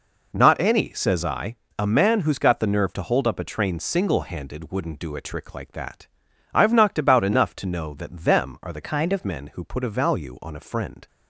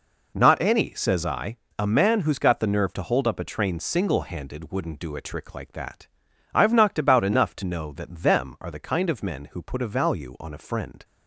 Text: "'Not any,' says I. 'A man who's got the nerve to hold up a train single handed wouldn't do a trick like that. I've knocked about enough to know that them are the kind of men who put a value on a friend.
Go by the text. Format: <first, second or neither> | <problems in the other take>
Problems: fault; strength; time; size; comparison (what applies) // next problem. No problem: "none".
second | changes voice from "kind" to "of"; from 8.8 to 9.2 s; 0.4 s long